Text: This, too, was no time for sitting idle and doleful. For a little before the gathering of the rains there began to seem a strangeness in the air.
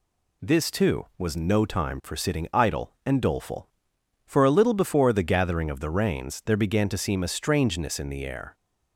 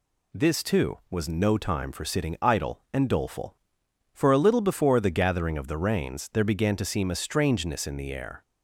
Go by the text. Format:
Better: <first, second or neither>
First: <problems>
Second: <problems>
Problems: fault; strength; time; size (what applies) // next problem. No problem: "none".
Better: neither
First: none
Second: none